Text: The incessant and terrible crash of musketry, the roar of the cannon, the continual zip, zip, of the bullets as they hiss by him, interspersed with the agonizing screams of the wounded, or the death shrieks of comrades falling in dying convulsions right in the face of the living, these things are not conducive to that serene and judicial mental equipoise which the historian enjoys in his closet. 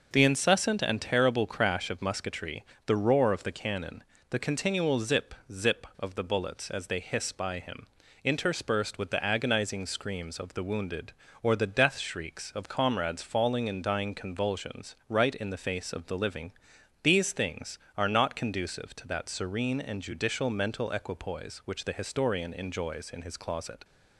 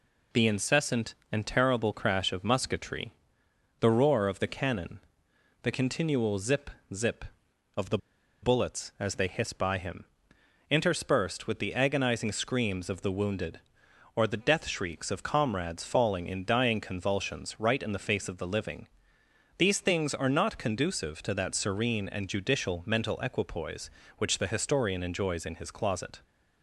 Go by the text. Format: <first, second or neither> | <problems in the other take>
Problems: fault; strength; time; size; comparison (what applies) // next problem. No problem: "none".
first | pauses between "the" and "bullets"; at 7.9 s; 0.45 s long